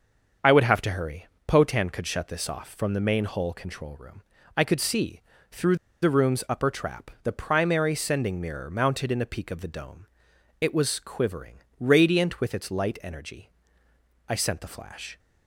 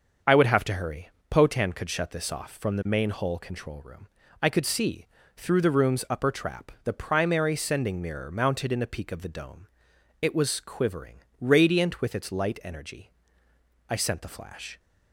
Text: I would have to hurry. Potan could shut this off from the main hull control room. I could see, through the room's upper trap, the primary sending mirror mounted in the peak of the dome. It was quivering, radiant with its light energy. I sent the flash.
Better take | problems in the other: second | starts louder than the rest; until 1.6 s; 6.5 dB; also in the second // pauses between "through" and "the"; slight; at 5.7 s; 0.26 s long

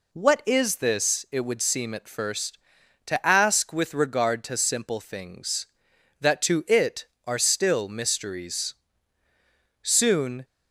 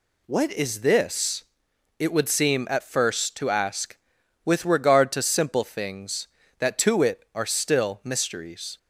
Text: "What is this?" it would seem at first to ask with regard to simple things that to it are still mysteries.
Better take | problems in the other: second | goes on to say "Soon"; noticeable; from 9.8 s on; 0.62 s long

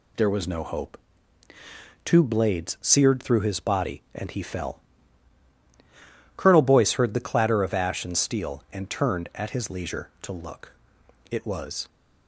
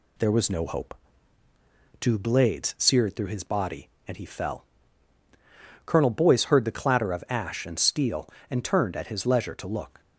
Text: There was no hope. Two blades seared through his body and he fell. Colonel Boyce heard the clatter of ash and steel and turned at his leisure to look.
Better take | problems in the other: second | goes on to say "It was"; from 11.3 s on; 0.58 s long

